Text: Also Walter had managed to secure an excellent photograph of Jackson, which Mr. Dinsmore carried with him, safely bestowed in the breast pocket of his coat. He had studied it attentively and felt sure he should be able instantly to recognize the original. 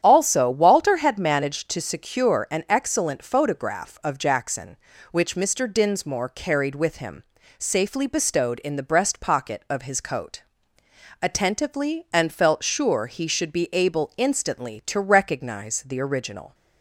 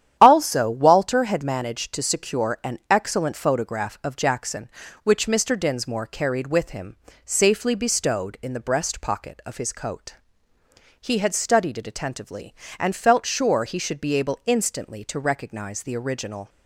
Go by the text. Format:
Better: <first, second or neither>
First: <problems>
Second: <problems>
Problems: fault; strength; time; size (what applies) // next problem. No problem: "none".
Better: second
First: starts louder than the rest; strong; until 1.0 s; 9.5 dB // skips "He had studied it"; at 10.8 s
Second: starts louder than the rest; strong; until 1.2 s; 10.5 dB